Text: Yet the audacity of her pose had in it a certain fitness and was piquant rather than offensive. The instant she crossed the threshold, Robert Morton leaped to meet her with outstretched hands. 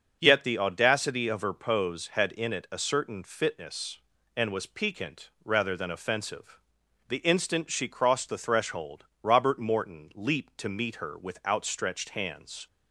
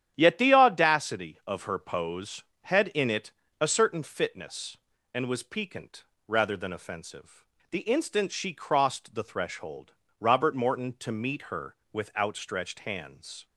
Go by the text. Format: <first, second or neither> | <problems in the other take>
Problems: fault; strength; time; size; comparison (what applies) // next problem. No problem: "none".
first | starts louder than the rest; strong; until 1.1 s; 10 dB; also in the first // pauses between "it" and "a"; slight; at 3.3 s; 0.28 s long // pauses between "piquant" and "rather"; slight; at 6.0 s; 0.24 s long; slight in the first // skips "leaped"; at 10.9 s